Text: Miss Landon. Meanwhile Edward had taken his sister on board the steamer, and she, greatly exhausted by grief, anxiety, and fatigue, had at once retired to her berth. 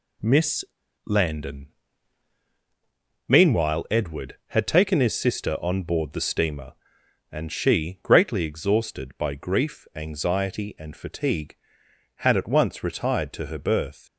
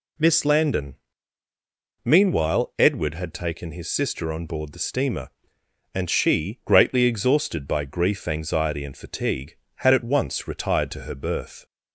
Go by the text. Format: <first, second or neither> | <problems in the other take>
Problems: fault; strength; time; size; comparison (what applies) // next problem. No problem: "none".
second | pauses between "Miss" and "Landon"; at 0.6 s; 0.38 s long